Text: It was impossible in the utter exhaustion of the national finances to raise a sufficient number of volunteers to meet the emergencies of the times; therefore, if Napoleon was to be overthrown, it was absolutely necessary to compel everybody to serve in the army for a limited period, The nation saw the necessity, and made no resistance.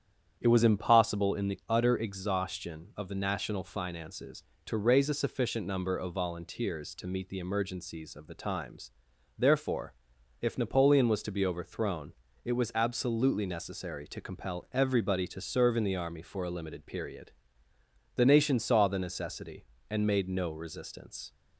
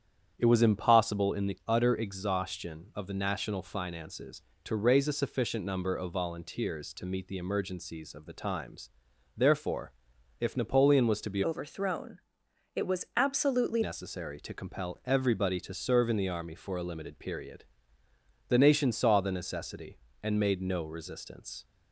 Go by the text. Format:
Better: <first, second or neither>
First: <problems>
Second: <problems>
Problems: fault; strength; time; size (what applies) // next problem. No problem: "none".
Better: first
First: starts louder than the rest; strong; until 1.4 s; 9 dB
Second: starts louder than the rest; strong; until 1.3 s; 9 dB // changes voice from "overthrown" to "absolutely"; from 11.4 to 13.8 s; 2.4 s long